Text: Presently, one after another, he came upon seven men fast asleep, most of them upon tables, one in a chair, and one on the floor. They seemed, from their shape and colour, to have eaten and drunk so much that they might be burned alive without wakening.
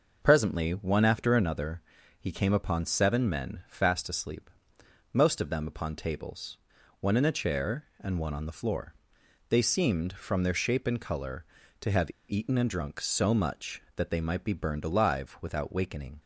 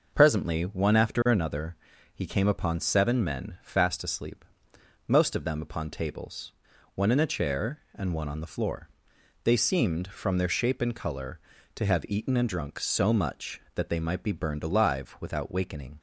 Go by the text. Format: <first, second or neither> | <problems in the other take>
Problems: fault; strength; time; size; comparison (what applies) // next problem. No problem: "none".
second | starts louder than the rest; noticeable; until 1.2 s; 6 dB; noticeable in the second // pauses between "have" and "eaten"; slight; at 12.1 s; 0.17 s long